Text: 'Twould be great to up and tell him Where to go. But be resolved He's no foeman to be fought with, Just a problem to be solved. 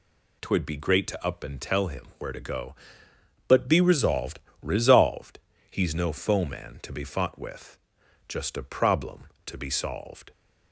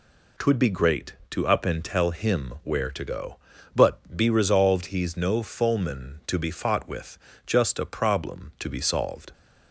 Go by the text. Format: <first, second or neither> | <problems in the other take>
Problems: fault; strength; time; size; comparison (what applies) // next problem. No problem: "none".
second | says "resolved" twice; at 4.6 s